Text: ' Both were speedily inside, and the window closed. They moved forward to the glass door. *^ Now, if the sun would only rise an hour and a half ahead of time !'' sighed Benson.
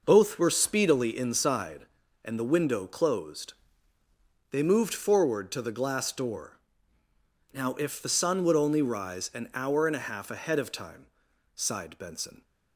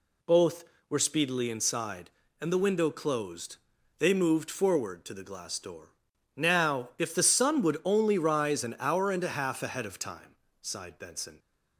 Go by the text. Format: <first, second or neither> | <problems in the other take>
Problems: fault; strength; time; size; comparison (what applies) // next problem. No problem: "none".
neither | none